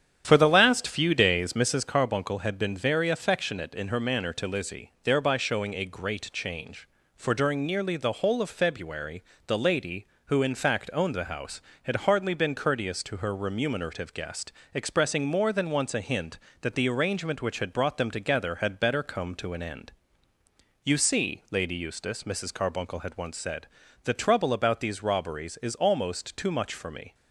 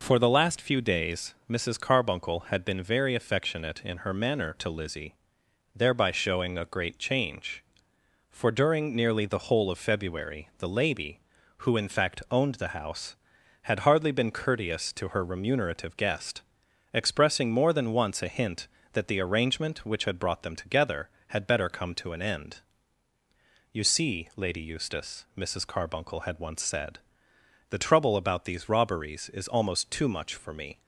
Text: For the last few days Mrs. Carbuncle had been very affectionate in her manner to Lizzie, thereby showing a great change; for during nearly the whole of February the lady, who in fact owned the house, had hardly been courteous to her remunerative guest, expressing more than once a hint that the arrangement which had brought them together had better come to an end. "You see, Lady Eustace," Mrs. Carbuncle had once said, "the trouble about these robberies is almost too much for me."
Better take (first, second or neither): second